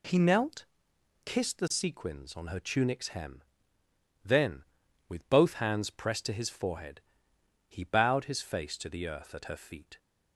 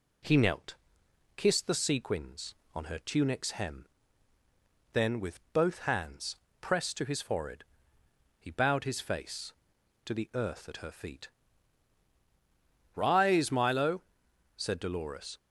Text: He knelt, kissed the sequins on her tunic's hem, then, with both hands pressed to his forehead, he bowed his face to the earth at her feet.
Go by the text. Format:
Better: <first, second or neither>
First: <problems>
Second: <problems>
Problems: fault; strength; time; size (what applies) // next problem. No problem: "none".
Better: first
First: none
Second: pauses between "hands" and "pressed"; slight; at 6.3 s; 0.26 s long // goes on to say "Rise Milo said Dolores"; strong; from 12.9 s on; 2.4 s long